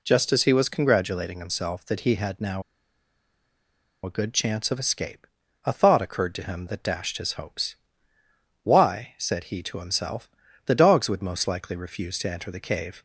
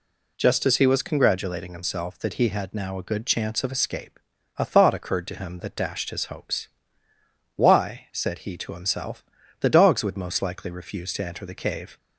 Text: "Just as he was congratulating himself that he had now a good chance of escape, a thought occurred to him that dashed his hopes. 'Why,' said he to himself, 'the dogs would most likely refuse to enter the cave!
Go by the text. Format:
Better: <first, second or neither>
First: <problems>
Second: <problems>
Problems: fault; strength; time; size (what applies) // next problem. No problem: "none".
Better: second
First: pauses between "now" and "a"; strong; at 2.6 s; 1.4 s long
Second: none